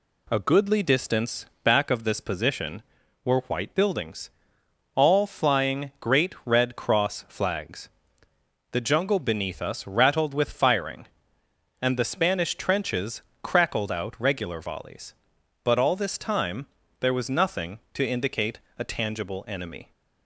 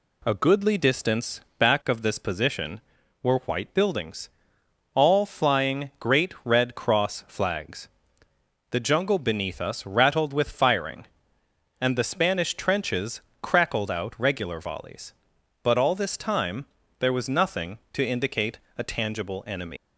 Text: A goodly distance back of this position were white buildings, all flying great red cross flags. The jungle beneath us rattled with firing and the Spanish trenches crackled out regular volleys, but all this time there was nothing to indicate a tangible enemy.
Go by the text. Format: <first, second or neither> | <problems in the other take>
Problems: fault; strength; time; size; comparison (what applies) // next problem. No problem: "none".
first | pauses between "distance" and "back"; slight; at 1.4 s; 0.18 s long; slight in the first // pauses between "trenches" and "crackled"; slight; at 13.2 s; 0.22 s long; slight in the first // pauses between "time" and "there"; slight; at 16.6 s; 0.34 s long; slight in the first // pauses between "indicate" and "a"; slight; at 18.5 s; 0.18 s long; slight in the first // leaves "enemy" unfinished; at 19.7 s; 135 ms